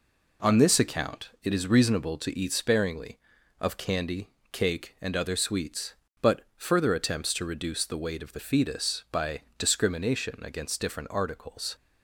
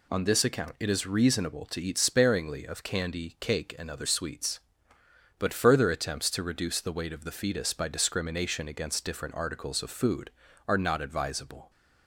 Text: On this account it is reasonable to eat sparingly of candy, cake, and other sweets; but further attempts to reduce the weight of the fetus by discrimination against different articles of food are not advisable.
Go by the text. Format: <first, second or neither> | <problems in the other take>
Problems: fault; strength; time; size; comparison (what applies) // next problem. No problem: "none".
second | pauses between "but" and "further"; slight; at 6.4 s; 0.16 s long // stops before "of food are not advisable"; at 11.7 s